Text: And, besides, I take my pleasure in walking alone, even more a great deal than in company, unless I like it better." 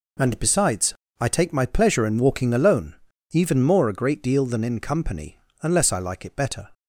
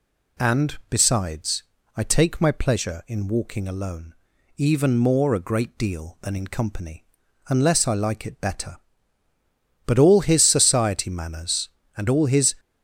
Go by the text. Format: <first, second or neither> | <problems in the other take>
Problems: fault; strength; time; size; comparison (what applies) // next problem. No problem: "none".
first | goes on to say "But all his society manners and all his"; strong; from 9.8 s on; 2.7 s long